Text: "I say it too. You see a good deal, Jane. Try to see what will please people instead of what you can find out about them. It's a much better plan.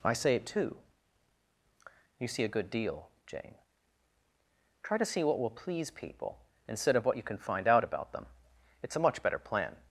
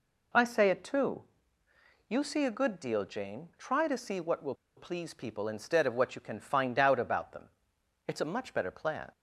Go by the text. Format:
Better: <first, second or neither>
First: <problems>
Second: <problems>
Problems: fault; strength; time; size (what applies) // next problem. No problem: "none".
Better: first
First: none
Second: pauses between "will" and "please"; slight; at 4.5 s; 0.21 s long